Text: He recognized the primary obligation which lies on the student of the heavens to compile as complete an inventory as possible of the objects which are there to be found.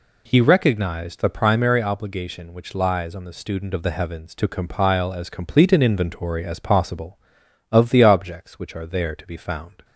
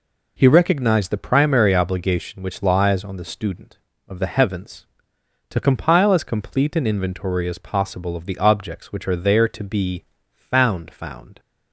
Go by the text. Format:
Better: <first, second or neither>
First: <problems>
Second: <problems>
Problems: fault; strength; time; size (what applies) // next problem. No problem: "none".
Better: first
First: none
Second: pauses between "be" and "found"; slight; at 10.0 s; 0.32 s long // says "found" twice; at 10.9 s